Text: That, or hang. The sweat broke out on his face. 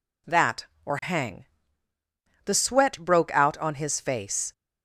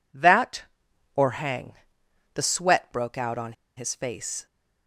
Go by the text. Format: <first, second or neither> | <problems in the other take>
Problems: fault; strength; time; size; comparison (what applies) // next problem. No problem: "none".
first | pauses between "on" and "his"; slight; at 3.5 s; 0.22 s long